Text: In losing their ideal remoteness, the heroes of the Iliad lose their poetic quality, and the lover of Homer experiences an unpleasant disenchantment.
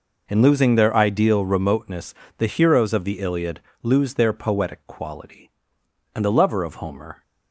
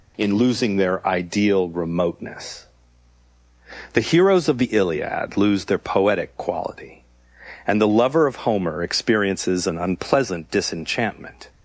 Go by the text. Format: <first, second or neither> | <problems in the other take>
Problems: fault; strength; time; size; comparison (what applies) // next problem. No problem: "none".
second | pauses between "Iliad" and "lose"; slight; at 3.6 s; 0.22 s long // stops before "experiences an unpleasant disenchantment"; at 7.2 s